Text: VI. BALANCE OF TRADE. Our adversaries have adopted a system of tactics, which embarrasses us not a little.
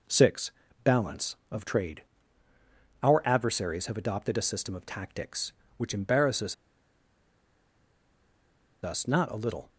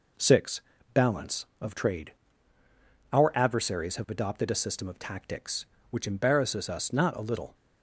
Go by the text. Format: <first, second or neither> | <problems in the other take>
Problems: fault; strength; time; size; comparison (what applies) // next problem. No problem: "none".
second | pauses between "embarrasses" and "us"; strong; at 6.5 s; 2.2 s long